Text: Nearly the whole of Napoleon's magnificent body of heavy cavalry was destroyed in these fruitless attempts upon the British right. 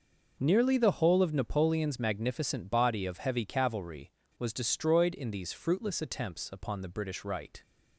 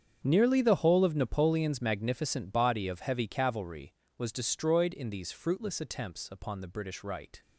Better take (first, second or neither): first